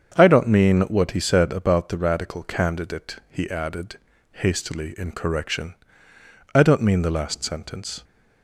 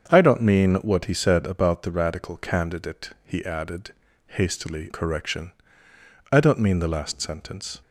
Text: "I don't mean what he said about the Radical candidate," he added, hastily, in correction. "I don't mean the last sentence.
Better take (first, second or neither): first